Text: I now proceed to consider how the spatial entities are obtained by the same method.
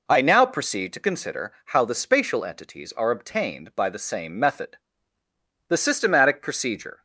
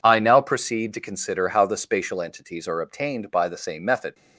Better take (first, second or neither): second